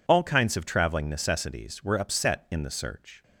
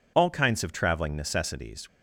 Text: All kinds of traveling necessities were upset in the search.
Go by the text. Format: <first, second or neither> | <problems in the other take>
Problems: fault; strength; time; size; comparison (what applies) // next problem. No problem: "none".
first | stops before "were upset in the search"; at 1.8 s